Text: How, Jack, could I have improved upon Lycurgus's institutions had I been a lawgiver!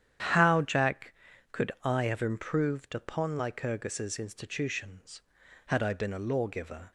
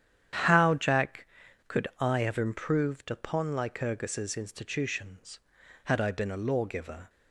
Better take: neither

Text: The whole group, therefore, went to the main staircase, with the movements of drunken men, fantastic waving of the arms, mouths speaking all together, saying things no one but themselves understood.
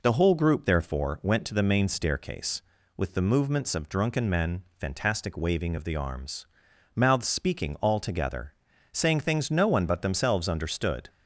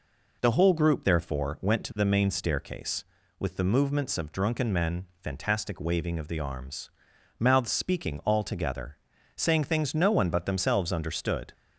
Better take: neither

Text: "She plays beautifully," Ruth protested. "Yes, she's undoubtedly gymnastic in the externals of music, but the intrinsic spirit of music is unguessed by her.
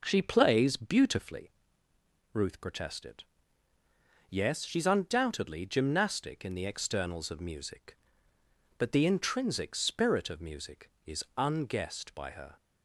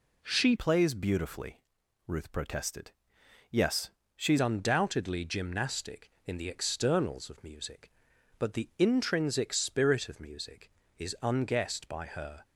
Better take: first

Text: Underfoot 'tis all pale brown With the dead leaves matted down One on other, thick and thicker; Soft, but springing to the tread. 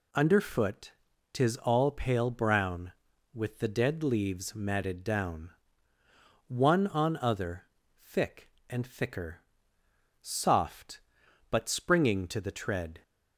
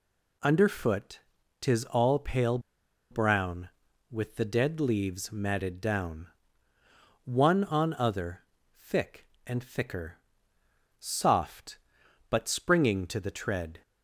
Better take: first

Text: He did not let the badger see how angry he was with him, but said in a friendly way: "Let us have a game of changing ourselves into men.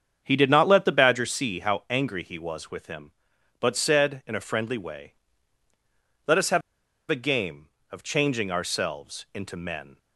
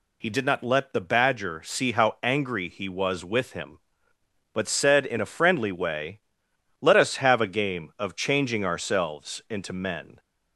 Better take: second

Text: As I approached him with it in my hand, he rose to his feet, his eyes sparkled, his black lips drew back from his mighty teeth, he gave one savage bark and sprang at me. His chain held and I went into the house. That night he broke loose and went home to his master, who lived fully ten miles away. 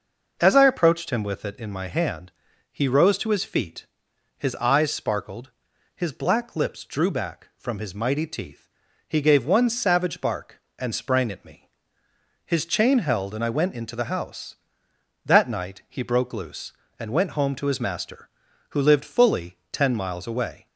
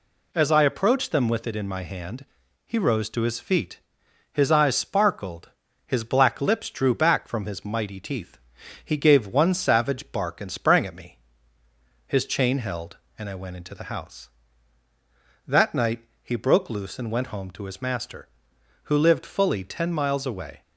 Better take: first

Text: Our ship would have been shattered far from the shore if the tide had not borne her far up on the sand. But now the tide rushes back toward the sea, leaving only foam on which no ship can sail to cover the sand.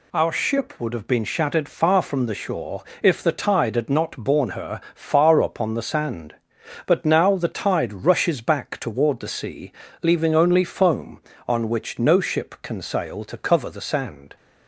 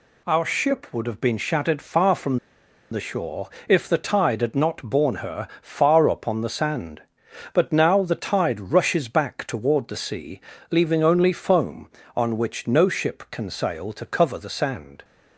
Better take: first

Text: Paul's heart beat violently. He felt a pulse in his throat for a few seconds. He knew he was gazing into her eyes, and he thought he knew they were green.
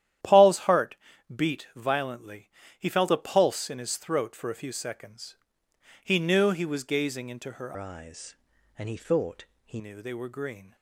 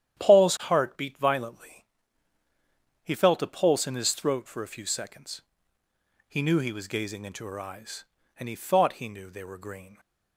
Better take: second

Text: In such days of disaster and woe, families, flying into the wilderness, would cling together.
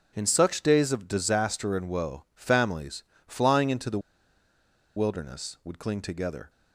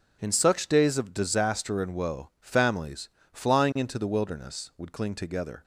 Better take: second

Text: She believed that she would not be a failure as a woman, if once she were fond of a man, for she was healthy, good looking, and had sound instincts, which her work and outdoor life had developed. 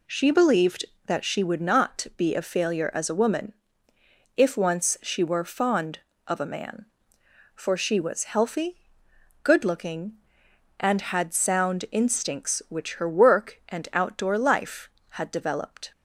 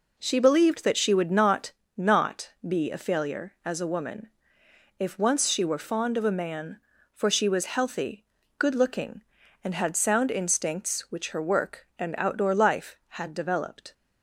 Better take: first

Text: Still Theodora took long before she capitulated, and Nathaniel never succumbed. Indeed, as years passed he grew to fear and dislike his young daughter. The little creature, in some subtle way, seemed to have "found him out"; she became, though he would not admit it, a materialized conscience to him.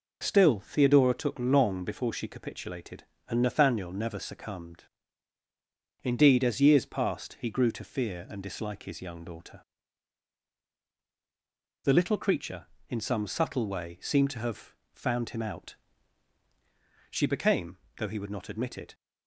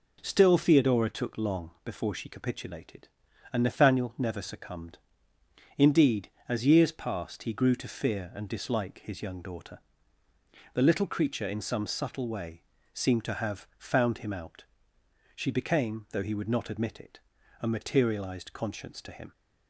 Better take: second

